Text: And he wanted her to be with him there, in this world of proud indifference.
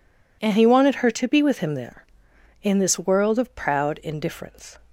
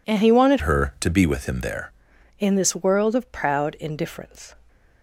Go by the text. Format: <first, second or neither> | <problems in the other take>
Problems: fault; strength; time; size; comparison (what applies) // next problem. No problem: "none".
first | changes voice from "her" to "there"; from 0.6 to 1.9 s; 1.3 s long